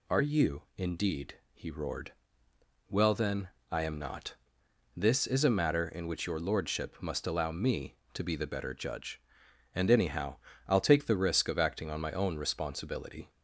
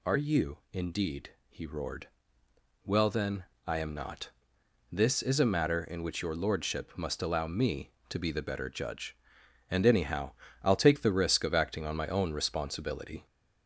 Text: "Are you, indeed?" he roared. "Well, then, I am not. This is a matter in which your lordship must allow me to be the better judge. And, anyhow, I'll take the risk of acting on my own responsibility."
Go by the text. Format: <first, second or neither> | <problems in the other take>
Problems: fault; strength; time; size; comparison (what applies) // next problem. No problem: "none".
first | gets louder; slight; throughout; 3 dB